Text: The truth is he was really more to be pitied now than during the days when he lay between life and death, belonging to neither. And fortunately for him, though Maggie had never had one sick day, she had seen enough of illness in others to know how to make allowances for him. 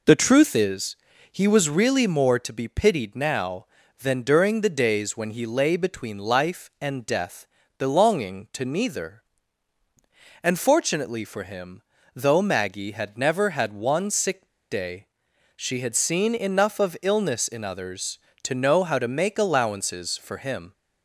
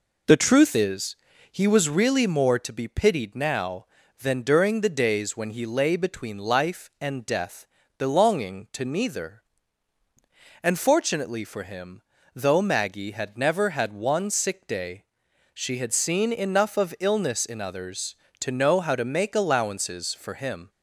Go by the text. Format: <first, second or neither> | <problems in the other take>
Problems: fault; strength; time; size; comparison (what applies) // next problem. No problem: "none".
second | pauses between "is" and "he"; slight; at 0.9 s; 0.34 s long; slight in the second // pauses between "sick" and "day"; slight; at 14.4 s; 0.24 s long